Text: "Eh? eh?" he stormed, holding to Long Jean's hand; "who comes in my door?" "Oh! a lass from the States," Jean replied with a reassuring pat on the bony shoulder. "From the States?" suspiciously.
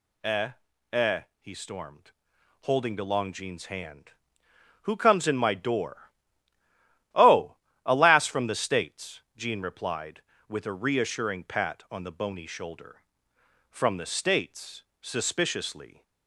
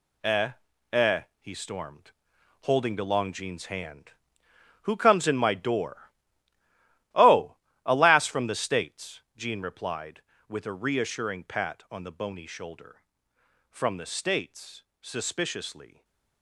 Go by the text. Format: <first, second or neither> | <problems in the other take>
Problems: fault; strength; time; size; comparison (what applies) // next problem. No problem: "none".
first | gets quieter; strong; throughout; 9 dB // stays silent after the last word; slight; from 15.8 s on; 0.6 s long